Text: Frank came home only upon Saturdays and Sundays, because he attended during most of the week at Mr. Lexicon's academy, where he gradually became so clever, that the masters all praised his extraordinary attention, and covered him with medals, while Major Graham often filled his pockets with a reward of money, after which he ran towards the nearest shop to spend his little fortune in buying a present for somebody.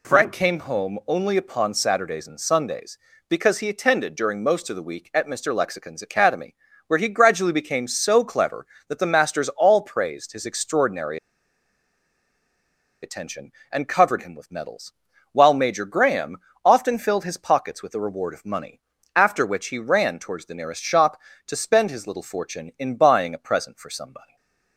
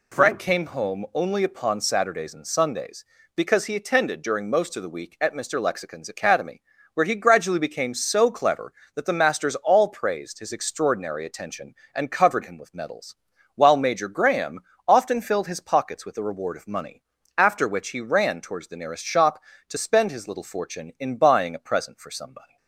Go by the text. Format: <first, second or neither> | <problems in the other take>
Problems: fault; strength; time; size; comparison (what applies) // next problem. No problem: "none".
second | pauses between "extraordinary" and "attention"; strong; at 11.1 s; 1.8 s long // pauses between "Graham" and "often"; slight; at 16.3 s; 0.28 s long; slight in the second // stays silent after the last word; slight; from 24.2 s on; 0.5 s long